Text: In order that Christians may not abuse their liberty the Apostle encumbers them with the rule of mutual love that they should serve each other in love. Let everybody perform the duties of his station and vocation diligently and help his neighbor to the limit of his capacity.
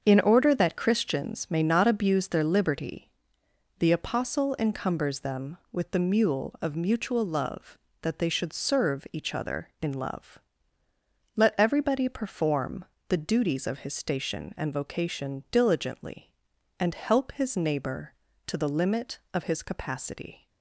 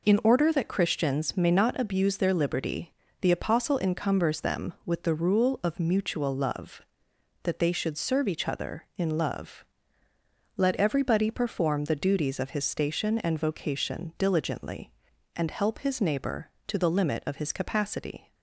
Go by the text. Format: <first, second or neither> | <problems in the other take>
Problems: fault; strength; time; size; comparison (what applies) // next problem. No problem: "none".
second | starts louder than the rest; until 1.0 s; 7 dB // pauses between "liberty" and "the"; noticeable; at 3.0 s; 0.70 s long; slight in the second // says "mule" for "rule"; at 5.9 s // pauses between "perform" and "the"; slight; at 12.8 s; 0.24 s long